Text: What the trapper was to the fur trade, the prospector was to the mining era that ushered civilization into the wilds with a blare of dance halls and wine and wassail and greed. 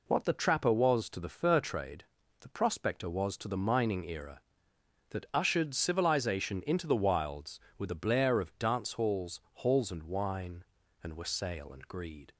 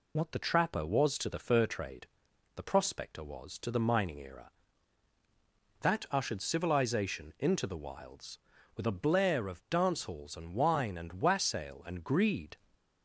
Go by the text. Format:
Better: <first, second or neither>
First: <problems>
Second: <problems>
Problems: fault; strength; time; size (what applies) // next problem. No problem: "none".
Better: second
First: says "halls" twice; at 9.5 s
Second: none